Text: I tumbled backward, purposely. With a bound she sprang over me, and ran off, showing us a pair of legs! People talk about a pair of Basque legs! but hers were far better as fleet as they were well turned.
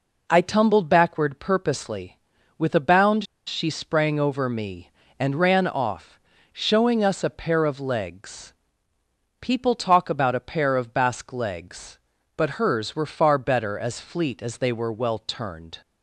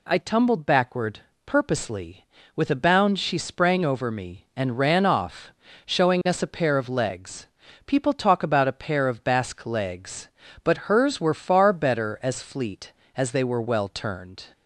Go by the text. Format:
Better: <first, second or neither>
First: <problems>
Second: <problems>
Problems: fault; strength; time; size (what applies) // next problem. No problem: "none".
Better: second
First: pauses between "bound" and "she"; slight; at 3.2 s; 0.23 s long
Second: none